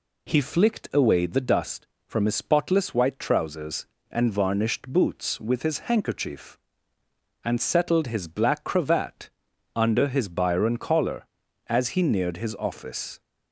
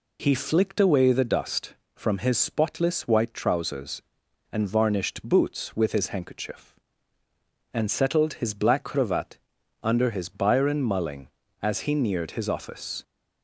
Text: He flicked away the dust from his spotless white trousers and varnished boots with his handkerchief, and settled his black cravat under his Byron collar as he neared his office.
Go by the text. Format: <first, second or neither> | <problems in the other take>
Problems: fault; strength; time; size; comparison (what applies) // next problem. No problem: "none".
first | pauses between "cravat" and "under"; at 9.3 s; 0.42 s long; also in the first // says "mulling" for "collar"; at 10.8 s